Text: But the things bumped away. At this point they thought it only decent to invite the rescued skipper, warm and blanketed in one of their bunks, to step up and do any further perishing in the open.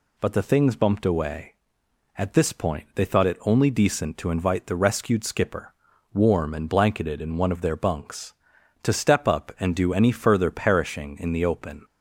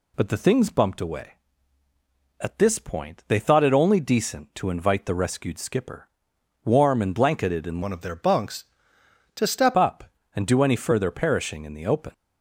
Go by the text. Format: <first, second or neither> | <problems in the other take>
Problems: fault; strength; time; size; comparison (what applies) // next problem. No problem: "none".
first | changes voice from "one" to "step"; from 7.8 to 9.7 s; 1.9 s long